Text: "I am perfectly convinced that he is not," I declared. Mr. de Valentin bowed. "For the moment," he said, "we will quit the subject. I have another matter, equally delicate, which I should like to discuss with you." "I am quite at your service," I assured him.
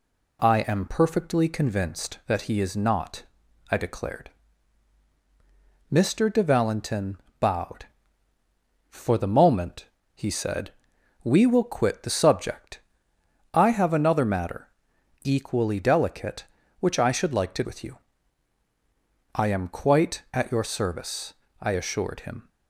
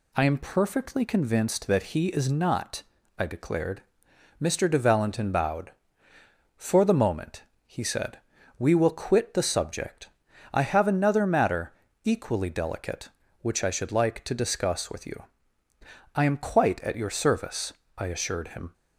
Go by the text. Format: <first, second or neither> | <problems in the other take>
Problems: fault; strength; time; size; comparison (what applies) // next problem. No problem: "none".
second | pauses between "Valentin" and "bowed"; slight; at 7.1 s; 0.22 s long // skips "discuss"; at 17.6 s